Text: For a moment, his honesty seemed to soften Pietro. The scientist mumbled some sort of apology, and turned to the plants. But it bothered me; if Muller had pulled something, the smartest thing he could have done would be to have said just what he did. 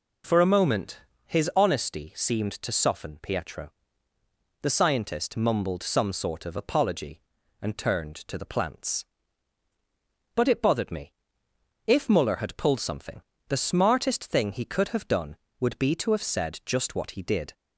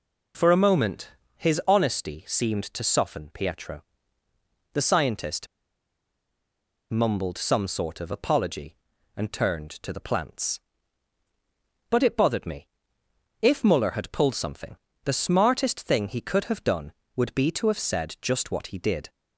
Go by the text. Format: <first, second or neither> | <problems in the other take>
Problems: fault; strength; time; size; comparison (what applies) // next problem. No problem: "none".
first | pauses between "scientist" and "mumbled"; strong; at 5.4 s; 1.4 s long